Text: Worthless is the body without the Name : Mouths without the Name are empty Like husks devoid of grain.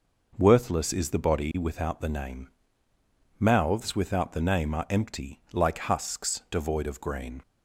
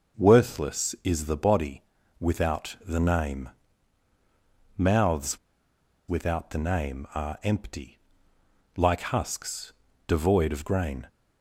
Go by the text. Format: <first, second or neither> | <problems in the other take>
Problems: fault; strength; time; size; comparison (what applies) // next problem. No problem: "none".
first | pauses between "body" and "without"; at 1.8 s; 0.38 s long // pauses between "Mouths" and "without"; noticeable; at 5.3 s; 0.71 s long // pauses between "empty" and "Like"; noticeable; at 7.9 s; 0.76 s long // pauses between "husks" and "devoid"; slight; at 9.7 s; 0.36 s long